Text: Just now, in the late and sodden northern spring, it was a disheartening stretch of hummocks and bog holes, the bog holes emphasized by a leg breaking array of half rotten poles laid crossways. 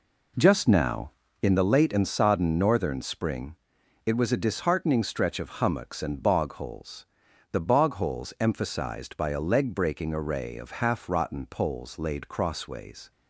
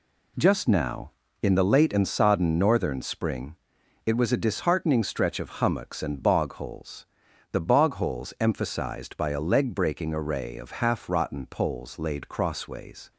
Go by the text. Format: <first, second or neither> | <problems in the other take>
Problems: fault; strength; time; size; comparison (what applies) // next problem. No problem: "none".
second | starts louder than the rest; until 1.6 s; 3.5 dB